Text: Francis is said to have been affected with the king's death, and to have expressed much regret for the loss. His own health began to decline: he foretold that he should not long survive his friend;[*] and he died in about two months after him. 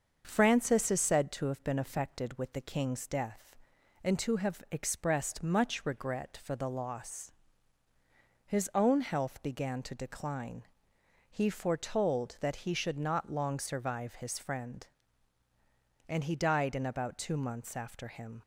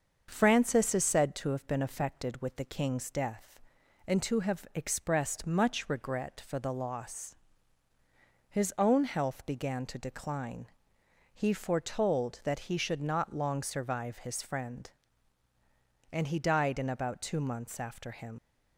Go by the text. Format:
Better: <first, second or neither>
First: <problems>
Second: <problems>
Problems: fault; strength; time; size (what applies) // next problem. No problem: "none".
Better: first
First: starts louder than the rest; until 1.2 s; 6.5 dB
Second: starts louder than the rest; until 1.3 s; 6.5 dB // leaves "him" unfinished; at 18.3 s; 70 ms